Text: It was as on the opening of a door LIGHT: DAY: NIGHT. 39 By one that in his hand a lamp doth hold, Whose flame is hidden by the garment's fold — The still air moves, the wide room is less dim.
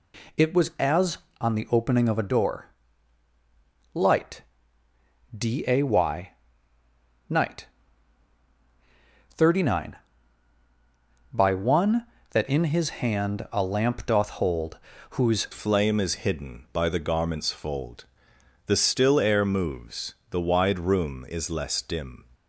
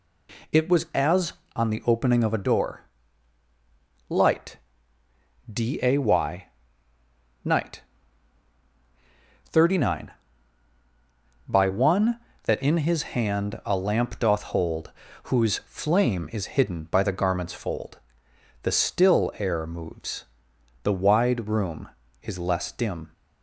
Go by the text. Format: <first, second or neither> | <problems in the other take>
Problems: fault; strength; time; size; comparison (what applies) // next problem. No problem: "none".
second | pauses between "door" and "LIGHT"; strong; at 2.6 s; 1.2 s long; strong in the second // changes voice at "flame"; from 15.5 s on; 6.7 s long